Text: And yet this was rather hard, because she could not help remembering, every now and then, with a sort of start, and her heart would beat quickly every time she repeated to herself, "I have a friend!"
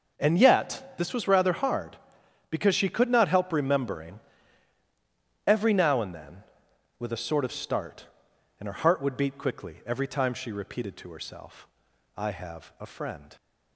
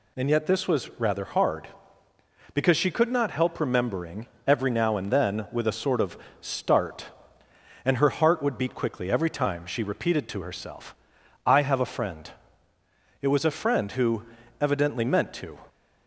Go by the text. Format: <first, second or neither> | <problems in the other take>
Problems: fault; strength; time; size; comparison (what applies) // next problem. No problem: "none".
first | pauses between "of" and "start"; slight; at 6.1 s; 0.22 s long // goes on to say "It was a friend who evidently meant to"; strong; from 13.2 s on; 2.4 s long